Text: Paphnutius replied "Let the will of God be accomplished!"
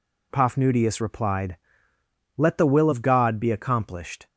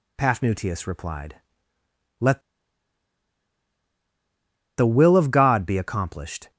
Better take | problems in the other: first | pauses between "replied" and "Let"; noticeable; at 1.3 s; 0.84 s long; noticeable in the first // pauses between "Let" and "the"; strong; at 2.3 s; 2.3 s long

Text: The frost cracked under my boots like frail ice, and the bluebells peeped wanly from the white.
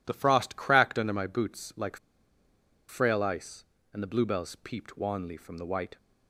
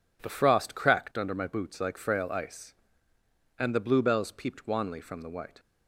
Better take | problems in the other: second | pauses between "like" and "frail"; noticeable; at 1.9 s; 0.91 s long

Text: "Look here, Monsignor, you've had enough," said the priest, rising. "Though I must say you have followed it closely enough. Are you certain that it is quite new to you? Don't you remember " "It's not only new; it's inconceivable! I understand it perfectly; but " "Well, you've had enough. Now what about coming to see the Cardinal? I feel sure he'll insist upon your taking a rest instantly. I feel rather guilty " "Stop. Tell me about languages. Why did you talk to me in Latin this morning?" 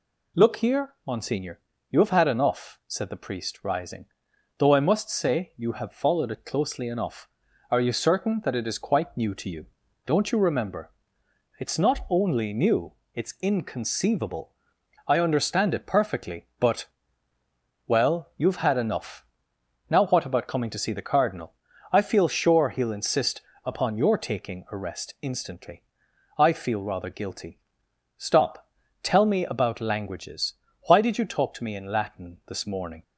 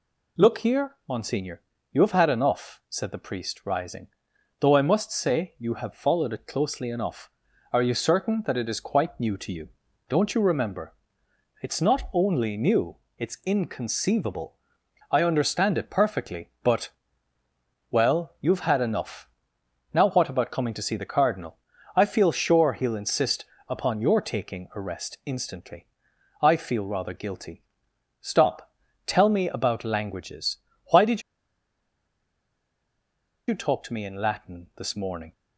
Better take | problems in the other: first | pauses between "insist" and "upon"; slight; at 23.4 s; 0.22 s long; slight in the first // pauses between "did" and "you"; strong; at 31.2 s; 2.2 s long

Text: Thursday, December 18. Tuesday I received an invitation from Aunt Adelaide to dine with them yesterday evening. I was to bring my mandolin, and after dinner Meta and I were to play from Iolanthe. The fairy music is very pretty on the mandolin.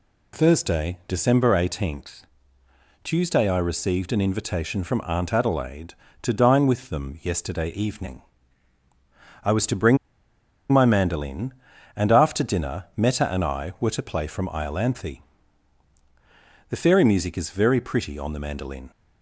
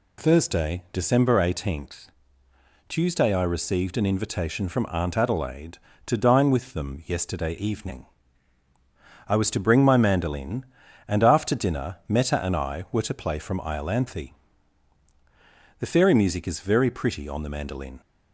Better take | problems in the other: second | pauses between "bring" and "my"; noticeable; at 9.9 s; 0.75 s long

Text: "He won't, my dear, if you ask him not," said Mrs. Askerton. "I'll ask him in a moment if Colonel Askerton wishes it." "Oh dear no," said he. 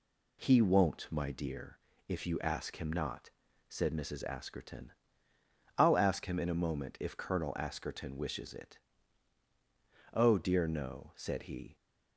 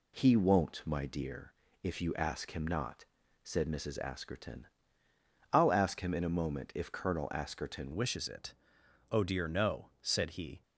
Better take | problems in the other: first | changes voice at "wishes"; from 7.9 s on; 2.7 s long

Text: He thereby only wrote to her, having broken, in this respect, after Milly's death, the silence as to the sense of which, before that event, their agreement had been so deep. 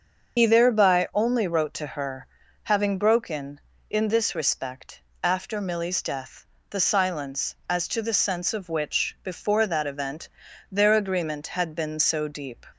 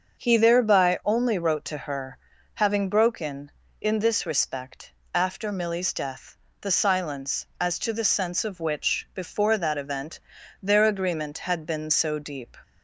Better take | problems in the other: second | loses the start of "He"; at 0.3 s; 80 ms // starts louder than the rest; until 1.4 s; 6.5 dB; also in the second

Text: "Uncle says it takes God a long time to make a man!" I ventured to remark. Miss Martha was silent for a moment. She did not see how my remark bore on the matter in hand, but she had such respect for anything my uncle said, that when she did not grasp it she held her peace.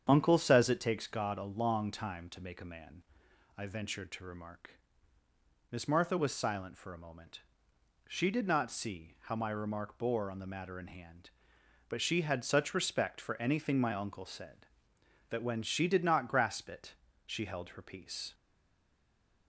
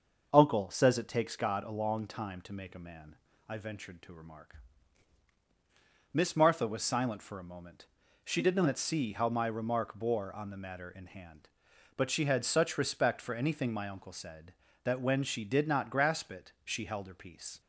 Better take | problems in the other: second | starts louder than the rest; strong; until 1.0 s; 8 dB; also in the second // pauses between "it" and "she"; slight; at 16.9 s; 0.32 s long // stays silent after the last word; from 18.3 s on; 1.1 s long

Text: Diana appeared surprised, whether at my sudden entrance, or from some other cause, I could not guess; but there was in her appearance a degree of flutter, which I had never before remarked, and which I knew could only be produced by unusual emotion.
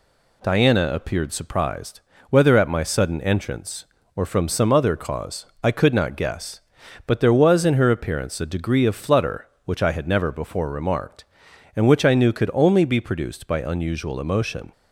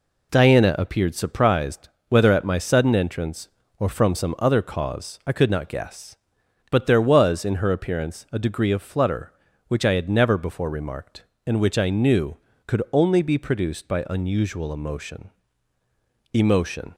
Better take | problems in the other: first | says "emotion" twice; at 16.3 s

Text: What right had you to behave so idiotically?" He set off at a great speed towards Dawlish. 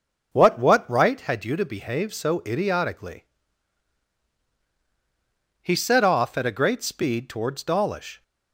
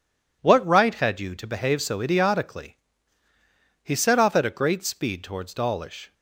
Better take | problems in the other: second | says "What" twice; at 0.5 s

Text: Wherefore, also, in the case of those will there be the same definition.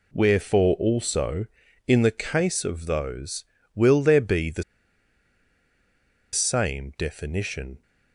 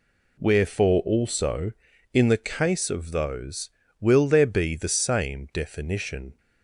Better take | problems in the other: second | pauses between "the" and "same"; strong; at 4.6 s; 1.7 s long

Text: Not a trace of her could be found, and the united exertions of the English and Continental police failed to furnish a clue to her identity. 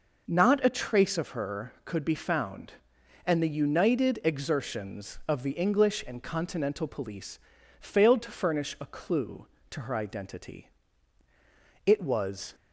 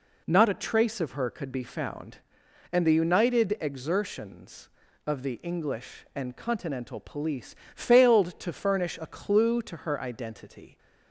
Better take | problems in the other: second | pauses between "police" and "failed"; at 7.3 s; 0.40 s long; slight in the second // goes on to say "It was"; noticeable; from 11.8 s on; 0.68 s long

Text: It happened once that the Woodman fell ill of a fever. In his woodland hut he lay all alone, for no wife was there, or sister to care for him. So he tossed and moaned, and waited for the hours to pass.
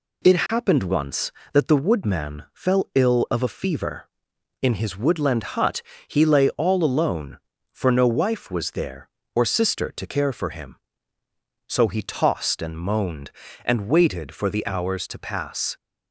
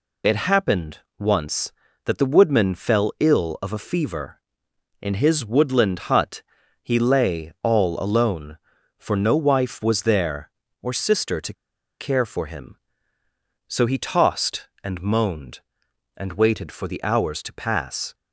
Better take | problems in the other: first | pauses between "happened" and "once"; slight; at 1.0 s; 0.18 s long // pauses between "hut" and "he"; at 6.4 s; 0.40 s long; slight in the first // pauses between "to" and "care"; noticeable; at 11.5 s; 0.46 s long

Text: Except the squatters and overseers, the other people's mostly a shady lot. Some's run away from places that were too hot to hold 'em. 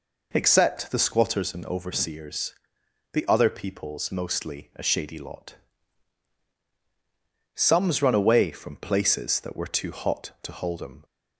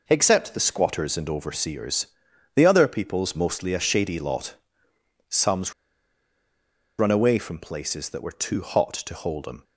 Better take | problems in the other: first | pauses between "Some's" and "run"; strong; at 5.7 s; 1.2 s long

